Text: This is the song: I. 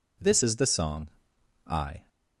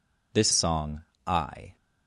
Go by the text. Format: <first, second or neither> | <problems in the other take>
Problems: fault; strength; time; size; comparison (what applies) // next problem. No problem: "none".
first | skips "is the"; at 0.5 s